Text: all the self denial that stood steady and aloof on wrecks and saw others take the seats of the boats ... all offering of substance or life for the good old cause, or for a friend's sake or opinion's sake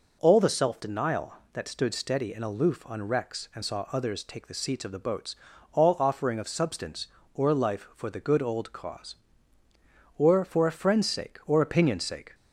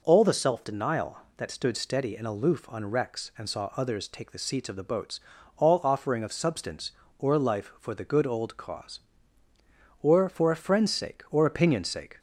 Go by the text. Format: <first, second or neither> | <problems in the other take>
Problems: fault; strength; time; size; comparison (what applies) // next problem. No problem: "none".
neither | none